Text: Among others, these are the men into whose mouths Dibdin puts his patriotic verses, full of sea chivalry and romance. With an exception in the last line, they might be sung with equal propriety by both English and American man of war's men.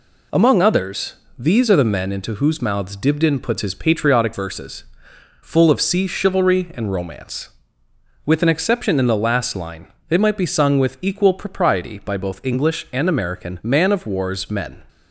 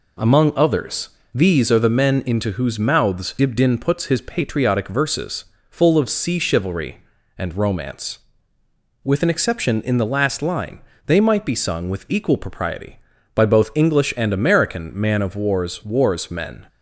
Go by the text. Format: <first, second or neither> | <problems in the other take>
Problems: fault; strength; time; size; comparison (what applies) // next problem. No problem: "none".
first | says "war's" twice; at 15.8 s